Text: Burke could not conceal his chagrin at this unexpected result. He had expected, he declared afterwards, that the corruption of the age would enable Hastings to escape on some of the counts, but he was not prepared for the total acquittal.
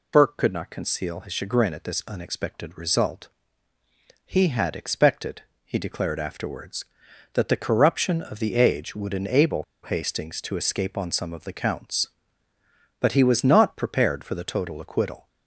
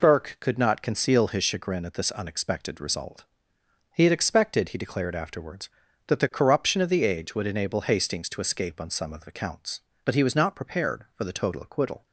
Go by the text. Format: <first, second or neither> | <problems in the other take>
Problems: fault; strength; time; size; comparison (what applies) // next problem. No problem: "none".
second | pauses between "enable" and "Hastings"; slight; at 9.6 s; 0.20 s long